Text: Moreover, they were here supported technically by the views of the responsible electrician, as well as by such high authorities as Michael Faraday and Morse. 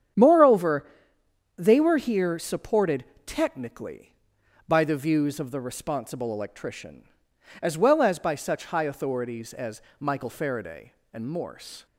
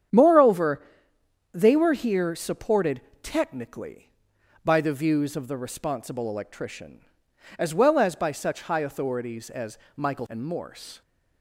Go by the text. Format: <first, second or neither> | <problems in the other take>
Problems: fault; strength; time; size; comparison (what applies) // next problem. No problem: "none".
first | starts louder than the rest; strong; until 1.8 s; 8.5 dB; strong in the first // pauses between "supported" and "technically"; slight; at 2.9 s; 0.22 s long; slight in the first // pauses between "as" and "Michael"; slight; at 9.7 s; 0.18 s long; slight in the first // skips "Faraday"; at 10.2 s